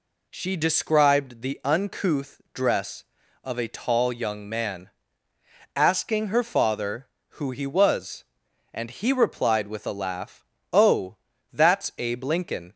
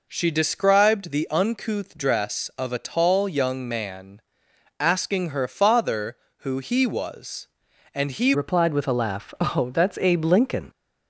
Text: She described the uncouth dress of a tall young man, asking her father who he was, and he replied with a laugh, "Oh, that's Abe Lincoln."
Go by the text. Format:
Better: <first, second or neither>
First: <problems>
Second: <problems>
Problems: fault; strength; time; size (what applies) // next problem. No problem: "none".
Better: first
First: none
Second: changes voice at "replied"; from 8.3 s on; 2.3 s long